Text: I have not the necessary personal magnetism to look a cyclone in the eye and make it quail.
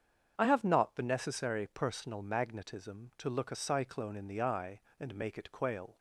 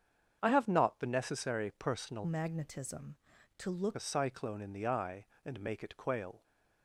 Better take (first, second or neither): first